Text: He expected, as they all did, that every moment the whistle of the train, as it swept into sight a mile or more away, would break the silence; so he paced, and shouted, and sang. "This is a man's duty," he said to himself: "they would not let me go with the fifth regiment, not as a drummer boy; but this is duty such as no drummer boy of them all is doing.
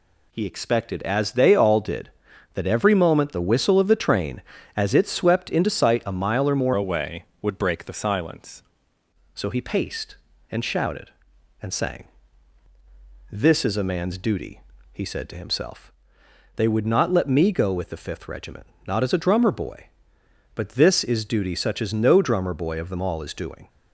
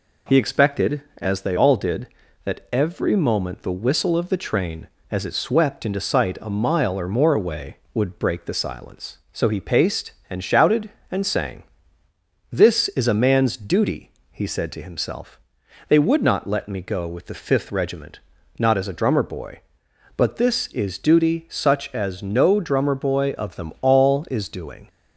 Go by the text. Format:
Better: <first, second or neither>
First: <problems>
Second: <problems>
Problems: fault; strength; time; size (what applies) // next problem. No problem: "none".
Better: second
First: changes voice from "away" to "silence"; from 6.7 to 8.6 s; 1.9 s long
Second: none